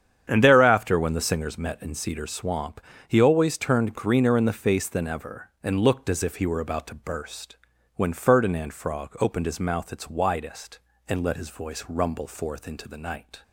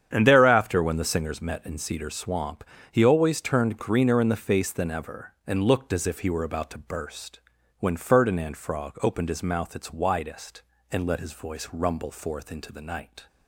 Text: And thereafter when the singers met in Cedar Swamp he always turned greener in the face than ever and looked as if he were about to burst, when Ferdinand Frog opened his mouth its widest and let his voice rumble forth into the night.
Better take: neither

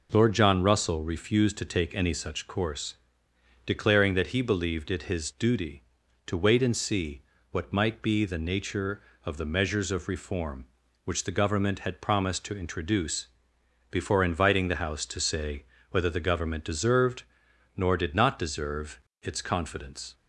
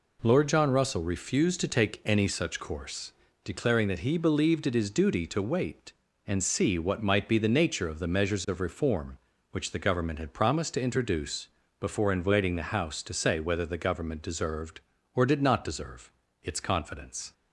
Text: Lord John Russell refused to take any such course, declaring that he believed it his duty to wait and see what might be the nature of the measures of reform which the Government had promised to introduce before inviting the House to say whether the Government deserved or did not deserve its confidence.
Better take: second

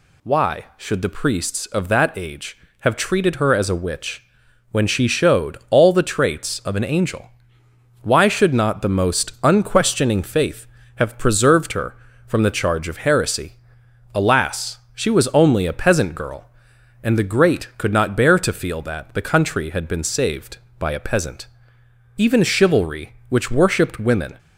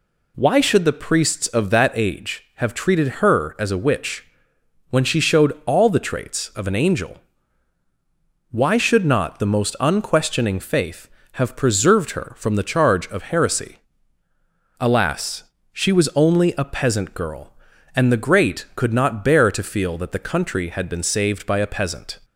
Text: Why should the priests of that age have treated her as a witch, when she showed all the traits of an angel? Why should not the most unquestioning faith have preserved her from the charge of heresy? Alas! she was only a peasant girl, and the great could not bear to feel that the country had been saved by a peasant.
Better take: second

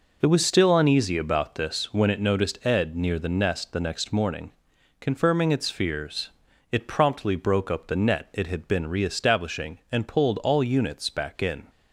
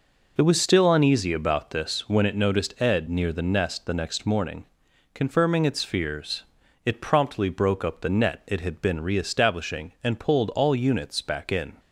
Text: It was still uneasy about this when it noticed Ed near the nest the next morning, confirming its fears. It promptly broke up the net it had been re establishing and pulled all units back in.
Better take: neither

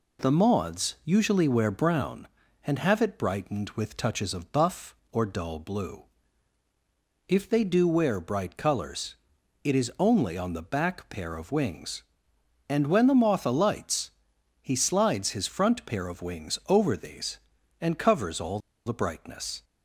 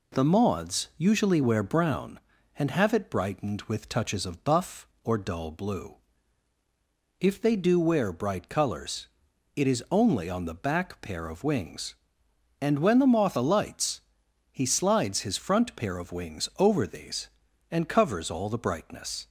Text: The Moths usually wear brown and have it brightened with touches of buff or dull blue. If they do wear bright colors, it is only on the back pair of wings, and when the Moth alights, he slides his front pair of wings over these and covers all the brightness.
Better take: second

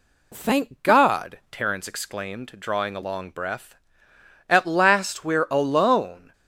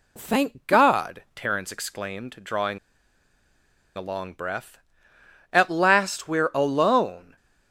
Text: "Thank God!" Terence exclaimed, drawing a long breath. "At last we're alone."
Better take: first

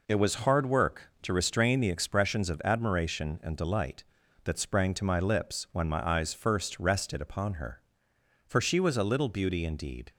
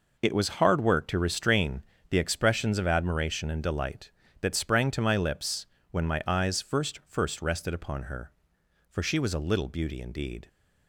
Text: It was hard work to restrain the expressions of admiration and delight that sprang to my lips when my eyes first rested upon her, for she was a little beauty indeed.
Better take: first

